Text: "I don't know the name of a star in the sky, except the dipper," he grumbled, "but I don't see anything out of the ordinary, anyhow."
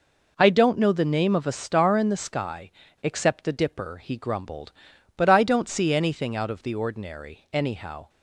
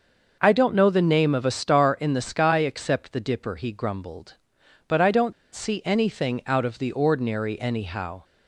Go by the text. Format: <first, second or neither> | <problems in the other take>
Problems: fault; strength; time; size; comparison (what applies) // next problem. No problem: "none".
first | starts louder than the rest; noticeable; until 1.4 s; 6 dB // pauses between "don't" and "see"; slight; at 5.3 s; 0.20 s long